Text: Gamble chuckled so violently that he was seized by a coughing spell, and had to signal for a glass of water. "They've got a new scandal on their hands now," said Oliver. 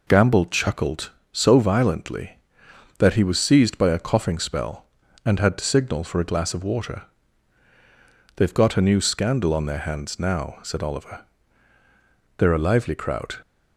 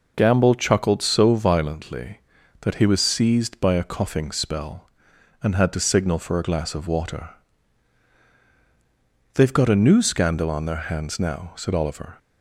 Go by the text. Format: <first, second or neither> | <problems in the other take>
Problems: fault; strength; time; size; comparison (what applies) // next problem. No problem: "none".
second | goes on to say "They're a lively crowd"; noticeable; from 12.3 s on; 0.98 s long